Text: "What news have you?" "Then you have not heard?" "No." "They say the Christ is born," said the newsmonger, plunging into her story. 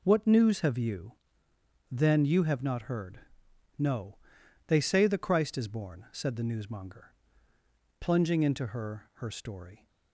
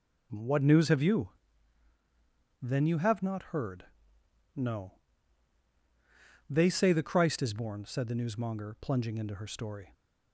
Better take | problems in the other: second | says "her" twice; at 9.1 s

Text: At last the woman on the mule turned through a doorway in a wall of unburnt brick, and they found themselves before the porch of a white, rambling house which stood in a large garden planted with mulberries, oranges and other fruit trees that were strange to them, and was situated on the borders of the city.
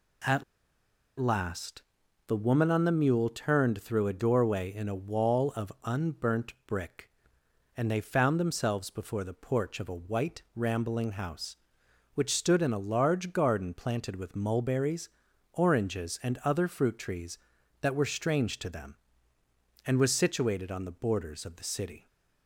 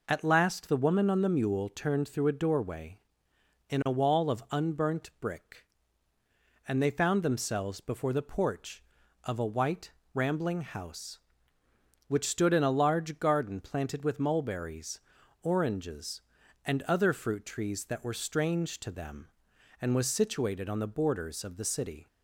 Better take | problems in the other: second | pauses between "At" and "last"; noticeable; at 0.4 s; 0.76 s long // pauses between "last" and "the"; at 1.8 s; 0.44 s long

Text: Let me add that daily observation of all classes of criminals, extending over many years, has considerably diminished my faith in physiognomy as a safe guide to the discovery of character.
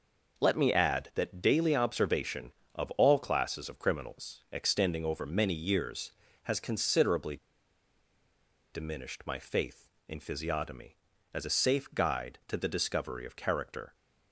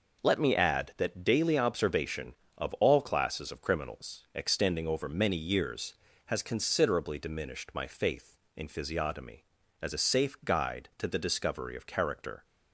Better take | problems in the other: second | pauses between "considerably" and "diminished"; strong; at 7.3 s; 1.3 s long

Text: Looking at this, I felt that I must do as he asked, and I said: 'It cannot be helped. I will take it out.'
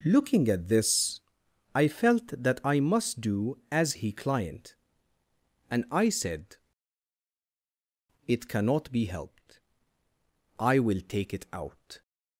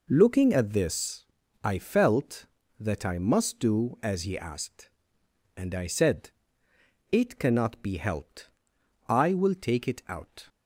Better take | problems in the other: second | says "client" for "asked"; at 4.1 s

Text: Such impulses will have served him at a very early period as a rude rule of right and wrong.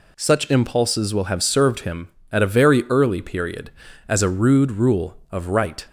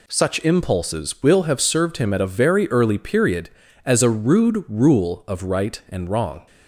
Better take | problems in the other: second | stops before "and wrong"; at 5.8 s

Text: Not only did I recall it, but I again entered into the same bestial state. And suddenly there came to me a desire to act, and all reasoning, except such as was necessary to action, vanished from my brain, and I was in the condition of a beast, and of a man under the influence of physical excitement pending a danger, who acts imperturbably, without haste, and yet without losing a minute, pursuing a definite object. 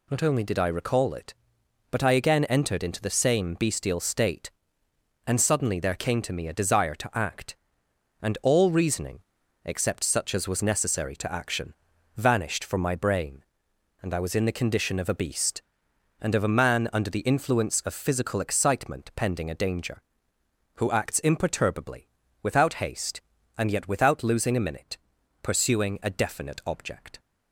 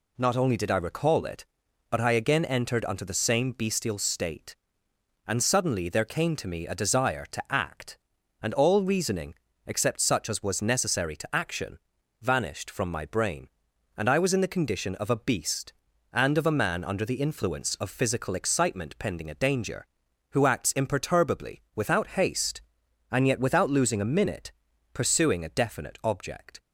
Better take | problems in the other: first | says "unto" for "into"; at 2.8 s

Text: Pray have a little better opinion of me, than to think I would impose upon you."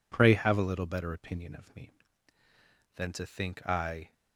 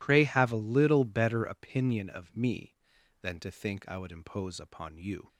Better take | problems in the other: second | stops before "would impose upon you"; at 4.1 s

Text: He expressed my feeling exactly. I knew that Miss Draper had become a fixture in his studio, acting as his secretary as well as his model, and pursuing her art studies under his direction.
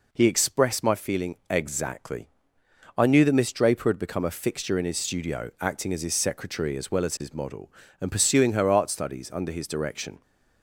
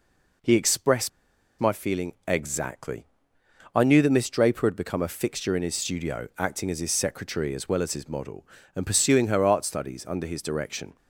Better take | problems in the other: first | pauses between "expressed" and "my"; noticeable; at 1.0 s; 0.50 s long

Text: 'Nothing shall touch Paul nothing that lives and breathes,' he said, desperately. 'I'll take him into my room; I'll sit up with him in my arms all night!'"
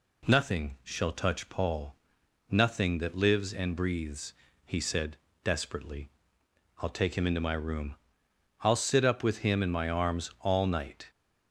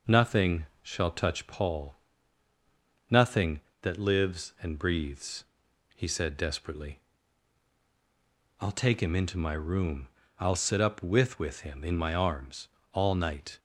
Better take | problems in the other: first | pauses between "Nothing" and "shall"; slight; at 0.6 s; 0.16 s long // pauses between "Paul" and "nothing"; at 1.9 s; 1.1 s long; noticeable in the first // says "with" twice; at 11.3 s // pauses between "arms" and "all"; slight; at 12.6 s; 0.24 s long

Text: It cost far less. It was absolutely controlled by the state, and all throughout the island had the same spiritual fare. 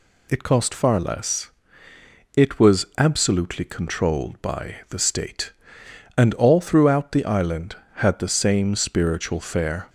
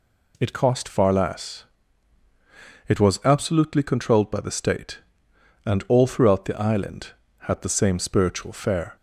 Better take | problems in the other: neither | none

